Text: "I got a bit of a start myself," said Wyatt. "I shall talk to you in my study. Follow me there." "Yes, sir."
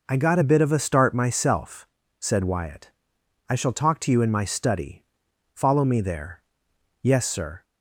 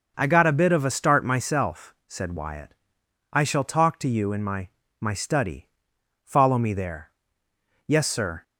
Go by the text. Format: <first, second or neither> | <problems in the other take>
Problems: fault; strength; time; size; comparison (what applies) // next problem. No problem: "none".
first | says "my" twice; at 4.9 s